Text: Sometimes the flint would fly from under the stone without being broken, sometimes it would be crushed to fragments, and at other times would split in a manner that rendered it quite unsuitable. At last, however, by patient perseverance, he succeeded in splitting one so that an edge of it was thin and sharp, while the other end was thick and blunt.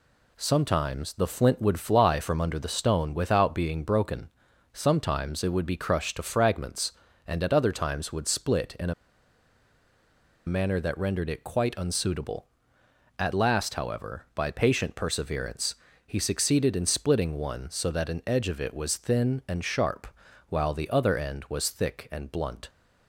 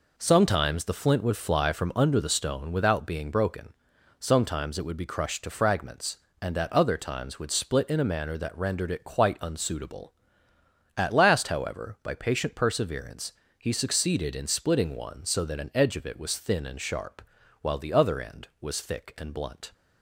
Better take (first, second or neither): second